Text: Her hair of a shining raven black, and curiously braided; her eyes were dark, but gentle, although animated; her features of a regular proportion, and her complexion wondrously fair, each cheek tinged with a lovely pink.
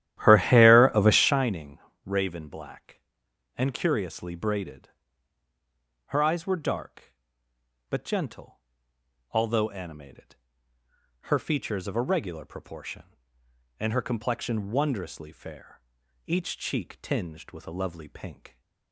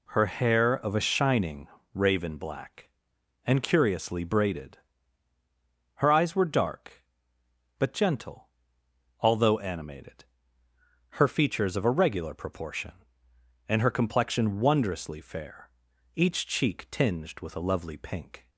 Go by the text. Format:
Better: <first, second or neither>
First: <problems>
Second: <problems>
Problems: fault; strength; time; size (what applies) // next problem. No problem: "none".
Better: second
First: starts louder than the rest; strong; until 1.5 s; 12.5 dB // pauses between "shining" and "raven"; slight; at 1.7 s; 0.26 s long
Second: pauses between "shining" and "raven"; slight; at 1.6 s; 0.26 s long